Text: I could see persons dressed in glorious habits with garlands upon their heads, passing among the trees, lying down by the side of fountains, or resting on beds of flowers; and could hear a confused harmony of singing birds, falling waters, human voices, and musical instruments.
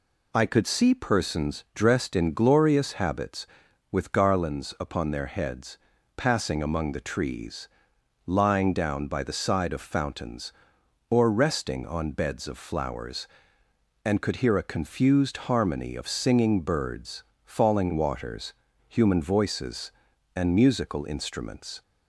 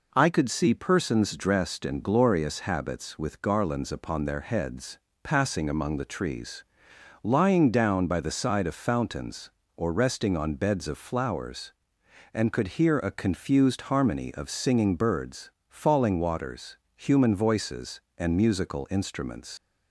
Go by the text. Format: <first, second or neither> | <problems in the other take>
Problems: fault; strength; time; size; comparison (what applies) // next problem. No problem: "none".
first | leaves "instruments" unfinished; at 19.5 s; 110 ms